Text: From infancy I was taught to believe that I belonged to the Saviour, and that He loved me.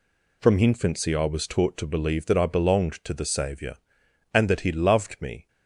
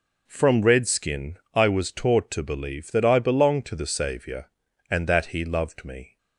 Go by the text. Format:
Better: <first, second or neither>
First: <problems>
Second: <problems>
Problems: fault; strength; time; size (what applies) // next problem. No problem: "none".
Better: first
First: none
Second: says "redskin" for "infancy"; at 0.6 s